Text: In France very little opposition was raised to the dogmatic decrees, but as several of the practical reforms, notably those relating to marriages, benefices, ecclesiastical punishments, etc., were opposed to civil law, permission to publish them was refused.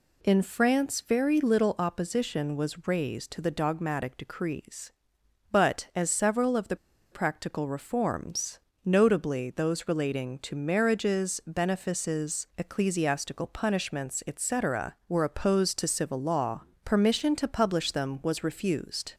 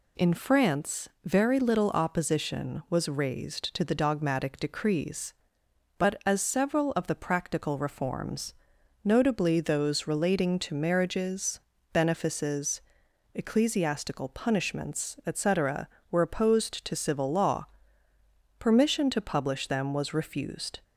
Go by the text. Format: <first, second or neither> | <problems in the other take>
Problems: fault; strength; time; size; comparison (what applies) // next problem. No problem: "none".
second | pauses between "the" and "practical"; at 6.7 s; 0.36 s long